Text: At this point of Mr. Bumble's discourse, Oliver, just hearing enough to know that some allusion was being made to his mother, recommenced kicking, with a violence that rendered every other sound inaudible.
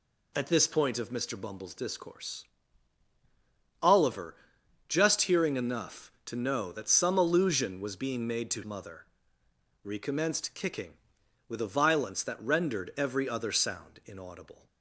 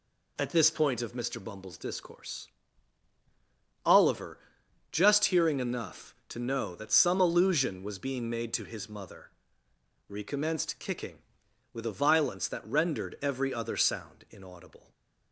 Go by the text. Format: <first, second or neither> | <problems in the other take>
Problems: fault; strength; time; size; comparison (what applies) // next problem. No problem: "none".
second | skips "his"; at 8.6 s